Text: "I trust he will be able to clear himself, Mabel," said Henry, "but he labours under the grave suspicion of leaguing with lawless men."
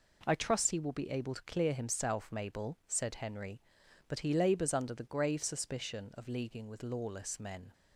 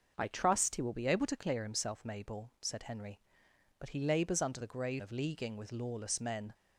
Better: first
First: none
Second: starts louder than the rest; noticeable; until 1.1 s; 6 dB // skips "suspicion"; at 5.0 s

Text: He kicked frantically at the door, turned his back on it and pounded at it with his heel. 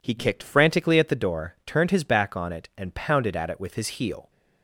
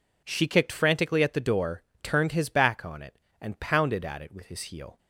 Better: first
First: none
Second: says "She" for "He"; at 0.2 s

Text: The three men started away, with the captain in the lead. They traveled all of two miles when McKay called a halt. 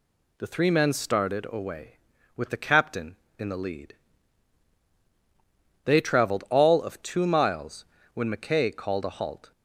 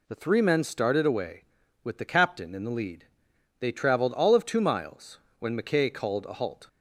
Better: neither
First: pauses between "miles" and "when"; slight; at 7.8 s; 0.28 s long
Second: pauses between "miles" and "when"; slight; at 5.1 s; 0.22 s long

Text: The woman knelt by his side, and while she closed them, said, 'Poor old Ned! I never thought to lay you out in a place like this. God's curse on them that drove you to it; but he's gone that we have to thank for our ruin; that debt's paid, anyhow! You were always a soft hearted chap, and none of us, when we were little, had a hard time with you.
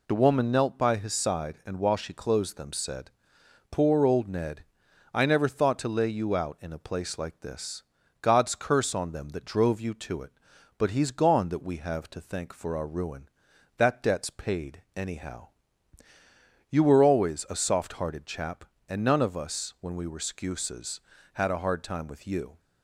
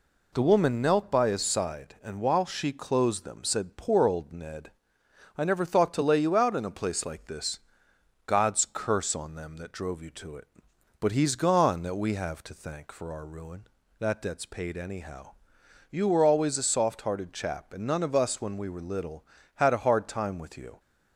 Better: second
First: says "skuses" for "little"; at 20.1 s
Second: none

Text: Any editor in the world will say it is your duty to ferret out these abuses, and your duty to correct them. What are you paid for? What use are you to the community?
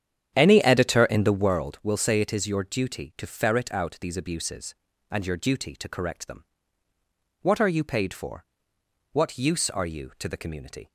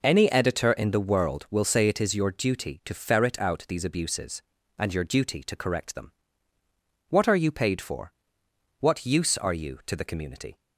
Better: second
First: starts louder than the rest; strong; until 1.6 s; 9 dB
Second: none

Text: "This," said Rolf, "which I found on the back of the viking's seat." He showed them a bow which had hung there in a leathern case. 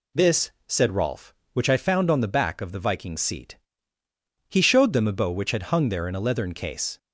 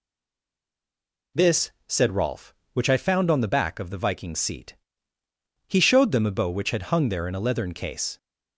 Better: first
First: none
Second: stays silent before the first word; noticeable; until 1.3 s; 1.3 s long

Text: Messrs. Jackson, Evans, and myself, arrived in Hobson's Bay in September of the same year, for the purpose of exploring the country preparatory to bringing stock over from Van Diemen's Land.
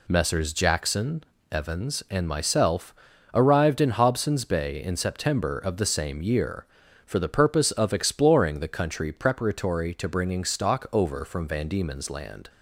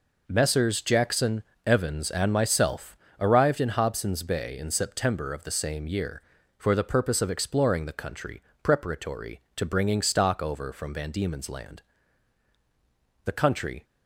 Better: first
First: none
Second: pauses between "country" and "preparatory"; slight; at 8.4 s; 0.22 s long // goes on to say "The country"; from 13.2 s on; 0.58 s long

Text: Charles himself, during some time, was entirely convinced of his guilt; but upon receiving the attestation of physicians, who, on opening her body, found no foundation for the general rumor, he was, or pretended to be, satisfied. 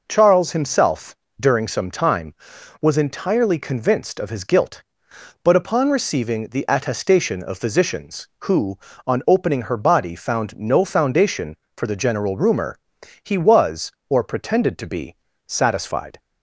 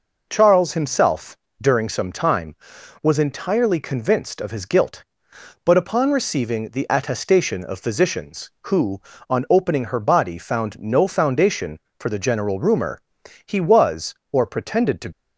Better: first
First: none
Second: stops before "be satisfied"; at 15.1 s

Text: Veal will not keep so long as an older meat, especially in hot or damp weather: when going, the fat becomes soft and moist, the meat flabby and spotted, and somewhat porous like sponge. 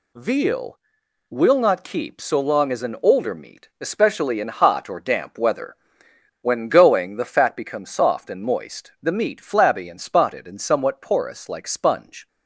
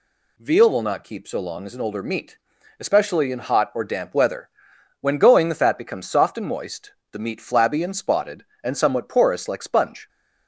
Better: neither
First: none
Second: none

